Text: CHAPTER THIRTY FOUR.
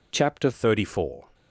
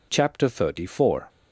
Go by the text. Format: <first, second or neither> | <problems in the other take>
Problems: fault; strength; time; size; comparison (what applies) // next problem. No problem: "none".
second | changes voice at "THIRTY"; from 0.5 s on; 0.7 s long